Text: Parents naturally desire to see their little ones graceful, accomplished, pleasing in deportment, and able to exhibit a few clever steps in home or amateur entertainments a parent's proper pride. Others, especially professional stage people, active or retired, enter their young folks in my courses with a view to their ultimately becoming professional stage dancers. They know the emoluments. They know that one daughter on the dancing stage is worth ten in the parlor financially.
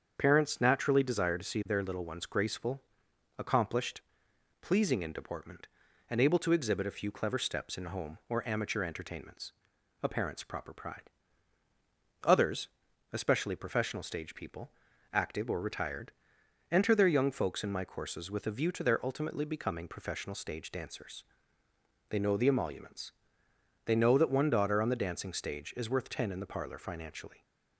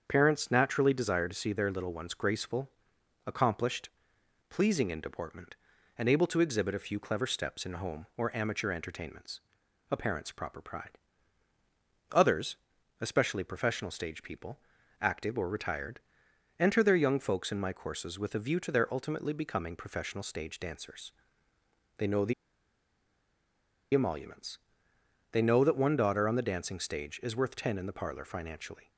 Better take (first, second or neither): first